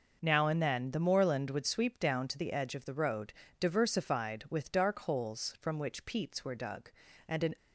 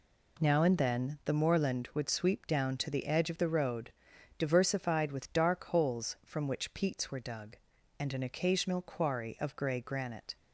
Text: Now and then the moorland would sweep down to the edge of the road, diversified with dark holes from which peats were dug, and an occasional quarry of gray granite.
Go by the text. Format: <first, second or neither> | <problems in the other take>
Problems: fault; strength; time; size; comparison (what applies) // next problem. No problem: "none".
second | stops before "occasional quarry of gray granite"; at 7.5 s